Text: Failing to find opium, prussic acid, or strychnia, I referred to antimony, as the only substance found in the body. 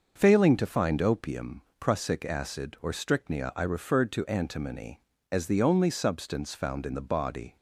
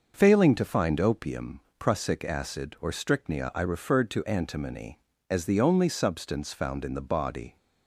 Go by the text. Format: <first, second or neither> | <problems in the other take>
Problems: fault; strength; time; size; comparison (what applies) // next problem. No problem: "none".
neither | starts louder than the rest; noticeable; the same in both